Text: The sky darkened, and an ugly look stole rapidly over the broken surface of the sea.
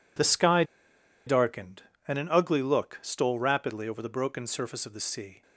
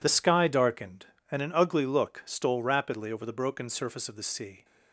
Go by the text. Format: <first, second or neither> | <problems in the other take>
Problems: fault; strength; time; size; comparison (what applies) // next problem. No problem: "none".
second | pauses between "sky" and "darkened"; noticeable; at 0.6 s; 0.63 s long